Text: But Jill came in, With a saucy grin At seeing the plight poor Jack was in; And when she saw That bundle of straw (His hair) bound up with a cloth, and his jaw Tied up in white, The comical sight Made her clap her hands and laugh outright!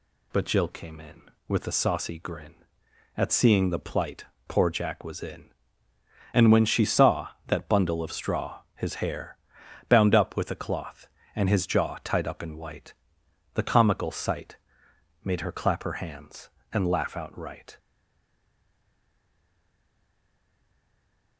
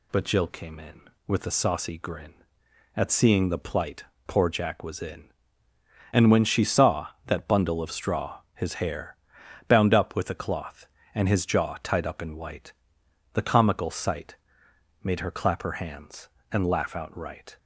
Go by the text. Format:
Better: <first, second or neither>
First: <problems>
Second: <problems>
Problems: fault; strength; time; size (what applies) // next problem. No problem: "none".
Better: second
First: pauses between "plight" and "poor"; slight; at 4.2 s; 0.24 s long // pauses between "sight" and "Made"; noticeable; at 14.5 s; 0.68 s long // stays silent after the last word; strong; from 17.7 s on; 3.6 s long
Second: pauses between "plight" and "poor"; slight; at 4.0 s; 0.24 s long // pauses between "sight" and "Made"; noticeable; at 14.3 s; 0.68 s long